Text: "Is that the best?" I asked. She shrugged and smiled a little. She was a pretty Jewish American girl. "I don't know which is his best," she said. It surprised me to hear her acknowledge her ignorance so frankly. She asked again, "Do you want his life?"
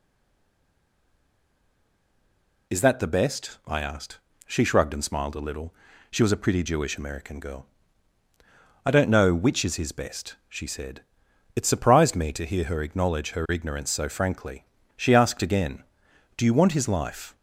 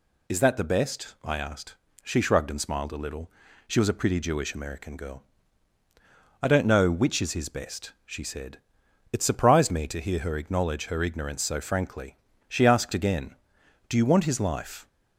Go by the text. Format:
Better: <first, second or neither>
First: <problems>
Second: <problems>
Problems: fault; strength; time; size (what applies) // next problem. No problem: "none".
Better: second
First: stays silent before the first word; strong; until 2.7 s; 2.7 s long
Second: none